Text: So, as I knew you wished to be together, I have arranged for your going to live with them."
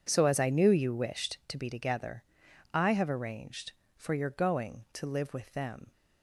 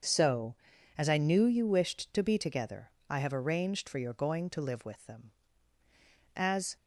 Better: first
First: none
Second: starts louder than the rest; until 1.4 s; 6.5 dB // goes on to say "As"; slight; from 6.3 s on; 0.40 s long

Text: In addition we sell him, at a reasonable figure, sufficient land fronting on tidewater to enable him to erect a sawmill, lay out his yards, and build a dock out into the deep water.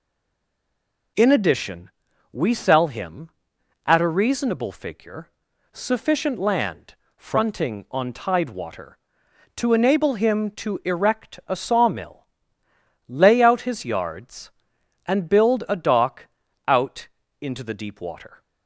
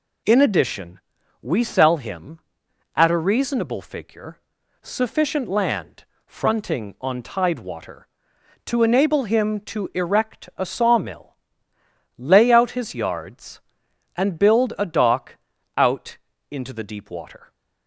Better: second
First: stays silent before the first word; until 1.1 s; 1.1 s long // pauses between "addition" and "we"; at 1.8 s; 0.42 s long // pauses between "land" and "fronting"; slight; at 6.9 s; 0.22 s long // pauses between "dock" and "out"; at 16.2 s; 0.40 s long // pauses between "out" and "into"; slight; at 17.0 s; 0.34 s long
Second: pauses between "addition" and "we"; at 0.9 s; 0.42 s long // pauses between "land" and "fronting"; slight; at 6.0 s; 0.22 s long // pauses between "dock" and "out"; at 15.3 s; 0.40 s long // pauses between "out" and "into"; slight; at 16.1 s; 0.34 s long

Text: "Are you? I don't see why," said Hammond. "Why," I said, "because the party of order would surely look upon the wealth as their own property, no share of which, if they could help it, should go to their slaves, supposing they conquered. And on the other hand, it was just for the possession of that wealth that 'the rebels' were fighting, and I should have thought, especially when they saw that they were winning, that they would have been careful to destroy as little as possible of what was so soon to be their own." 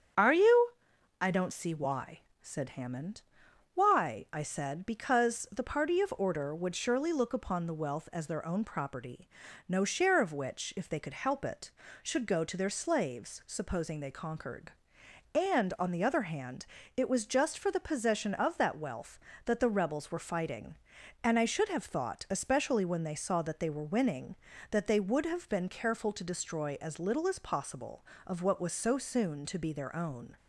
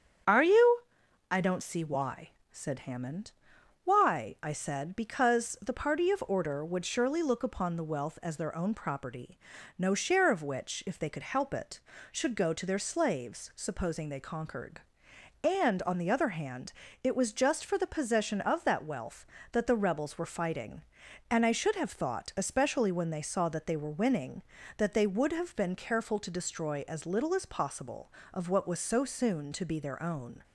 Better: neither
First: starts louder than the rest; strong; until 1.7 s; 8 dB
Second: starts louder than the rest; strong; until 1.8 s; 8 dB

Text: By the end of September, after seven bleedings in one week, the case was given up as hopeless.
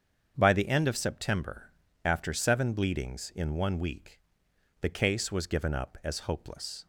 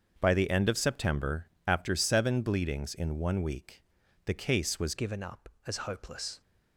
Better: first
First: starts louder than the rest; strong; until 1.3 s; 7.5 dB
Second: starts louder than the rest; until 1.1 s; 7 dB // changes voice at "given"; from 4.9 s on; 1.5 s long

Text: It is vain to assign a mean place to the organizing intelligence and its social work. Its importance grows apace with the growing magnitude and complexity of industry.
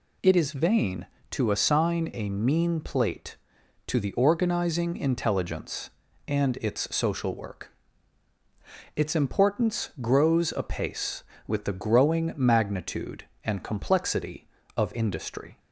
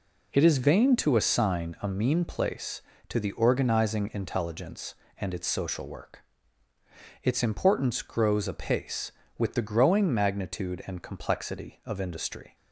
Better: second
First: says "plate" for "place"; at 2.7 s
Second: none

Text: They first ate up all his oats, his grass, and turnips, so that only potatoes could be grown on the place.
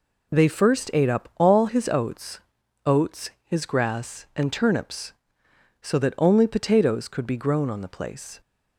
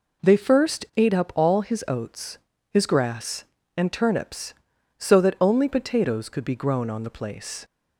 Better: second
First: says "oats" twice; at 2.8 s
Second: none

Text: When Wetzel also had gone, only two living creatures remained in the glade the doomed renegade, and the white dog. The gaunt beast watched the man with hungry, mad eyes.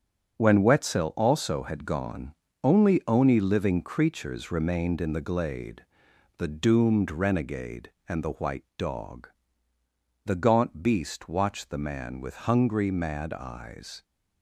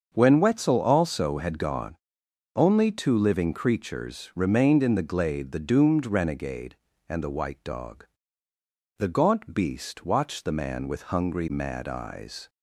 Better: second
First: starts louder than the rest; strong; until 1.4 s; 7 dB // says "oni" for "two"; at 3.0 s // pauses between "glade" and "the"; noticeable; at 5.8 s; 0.54 s long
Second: starts louder than the rest; until 1.1 s; 7 dB

